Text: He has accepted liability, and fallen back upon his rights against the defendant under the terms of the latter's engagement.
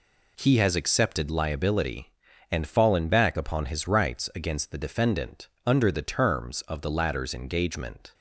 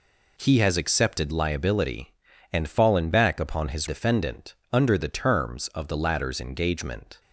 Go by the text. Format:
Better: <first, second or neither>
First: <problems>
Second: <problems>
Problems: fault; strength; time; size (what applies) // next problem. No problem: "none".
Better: first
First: pauses between "defendant" and "under"; slight; at 5.4 s; 0.18 s long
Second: skips "rights against the"; at 3.8 s // pauses between "defendant" and "under"; slight; at 4.5 s; 0.18 s long